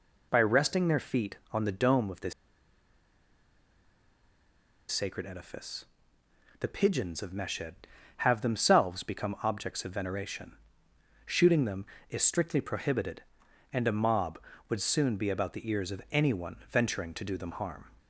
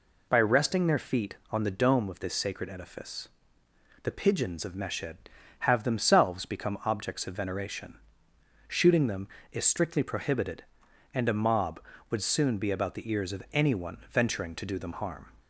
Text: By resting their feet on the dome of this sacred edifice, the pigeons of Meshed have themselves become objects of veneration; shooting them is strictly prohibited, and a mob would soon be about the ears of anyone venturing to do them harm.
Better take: second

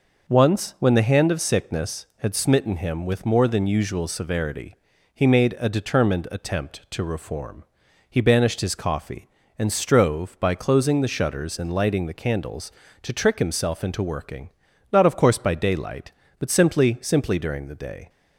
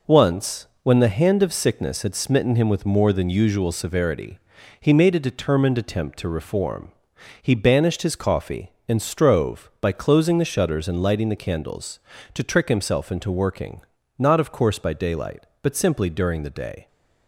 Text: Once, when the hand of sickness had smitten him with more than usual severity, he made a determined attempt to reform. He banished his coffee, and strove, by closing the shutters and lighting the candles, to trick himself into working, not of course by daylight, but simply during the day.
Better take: second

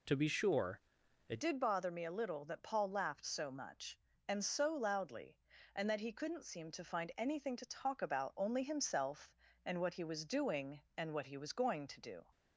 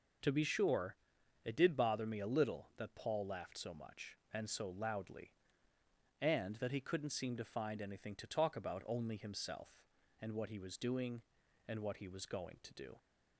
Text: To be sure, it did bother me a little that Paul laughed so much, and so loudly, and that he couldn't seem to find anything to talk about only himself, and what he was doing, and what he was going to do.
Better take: second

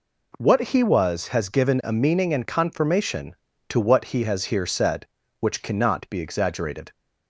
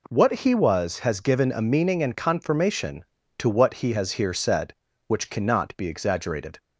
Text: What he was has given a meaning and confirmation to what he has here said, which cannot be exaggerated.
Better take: neither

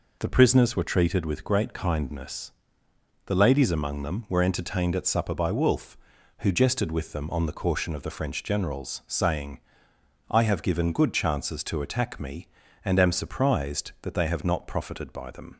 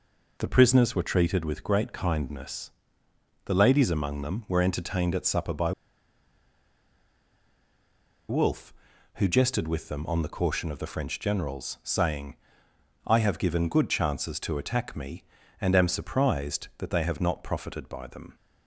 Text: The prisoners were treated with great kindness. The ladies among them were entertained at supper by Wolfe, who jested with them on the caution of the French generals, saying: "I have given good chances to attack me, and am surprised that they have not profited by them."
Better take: first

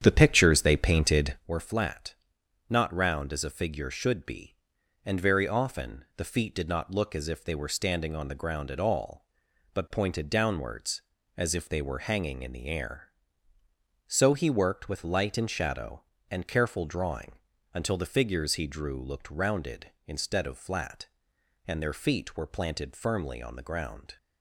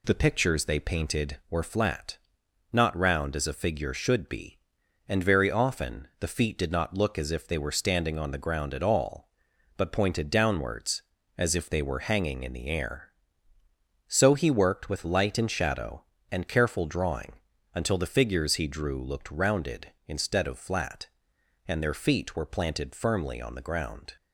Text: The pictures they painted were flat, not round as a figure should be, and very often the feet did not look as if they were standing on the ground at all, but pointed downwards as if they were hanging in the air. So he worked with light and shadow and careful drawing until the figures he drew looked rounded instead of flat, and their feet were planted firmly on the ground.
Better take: second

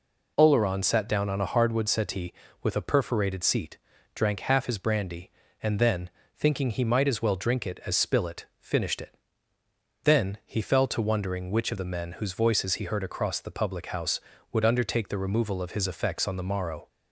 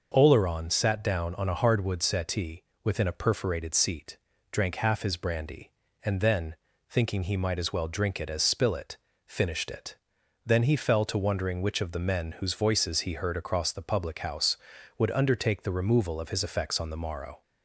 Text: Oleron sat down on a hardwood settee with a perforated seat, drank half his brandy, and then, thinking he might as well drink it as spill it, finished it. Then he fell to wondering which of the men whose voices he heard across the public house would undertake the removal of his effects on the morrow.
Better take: first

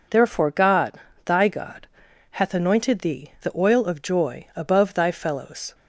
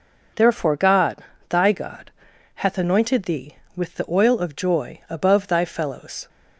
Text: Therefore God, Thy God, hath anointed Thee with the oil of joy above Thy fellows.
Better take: second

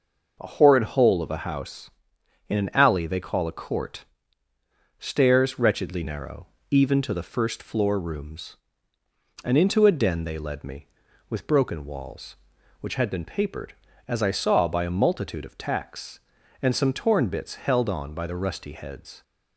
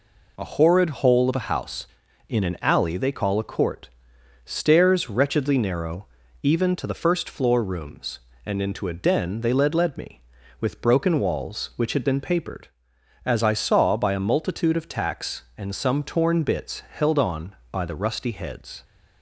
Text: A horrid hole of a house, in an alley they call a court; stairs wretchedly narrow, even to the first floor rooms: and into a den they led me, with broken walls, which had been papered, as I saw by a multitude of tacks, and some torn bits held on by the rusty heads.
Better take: first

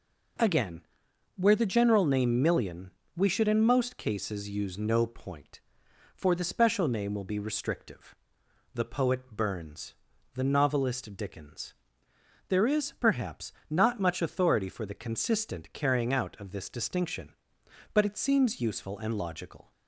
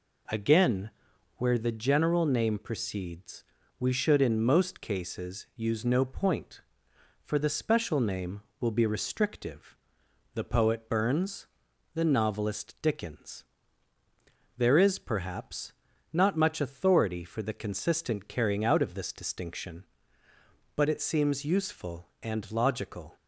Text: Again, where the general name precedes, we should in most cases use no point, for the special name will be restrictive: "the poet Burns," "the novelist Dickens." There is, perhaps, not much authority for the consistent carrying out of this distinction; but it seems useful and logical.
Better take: second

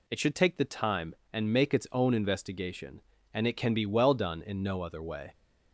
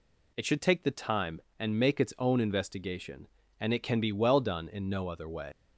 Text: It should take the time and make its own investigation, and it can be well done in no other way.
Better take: first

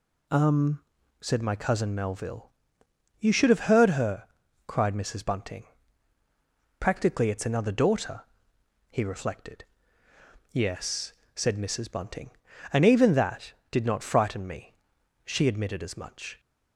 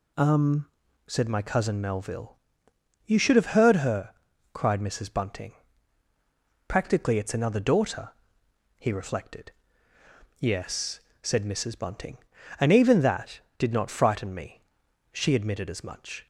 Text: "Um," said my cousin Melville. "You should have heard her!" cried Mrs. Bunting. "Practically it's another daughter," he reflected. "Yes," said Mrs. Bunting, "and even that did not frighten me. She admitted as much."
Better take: neither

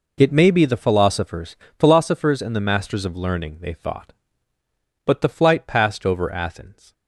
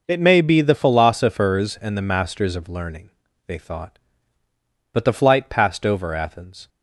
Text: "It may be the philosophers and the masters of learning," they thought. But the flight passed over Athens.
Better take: second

